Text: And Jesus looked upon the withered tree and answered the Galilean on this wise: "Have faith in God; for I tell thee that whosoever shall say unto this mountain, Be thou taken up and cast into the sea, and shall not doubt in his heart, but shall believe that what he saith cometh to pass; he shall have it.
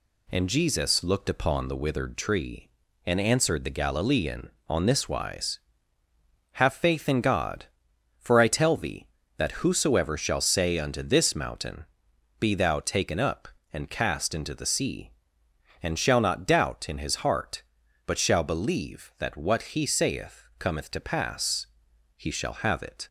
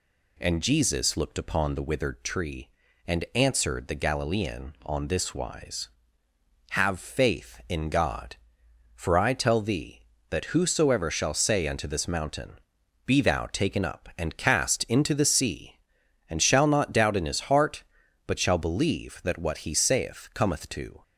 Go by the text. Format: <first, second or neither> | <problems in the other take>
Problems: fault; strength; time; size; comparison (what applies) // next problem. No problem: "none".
first | stops before "pass he shall have it"; at 21.0 s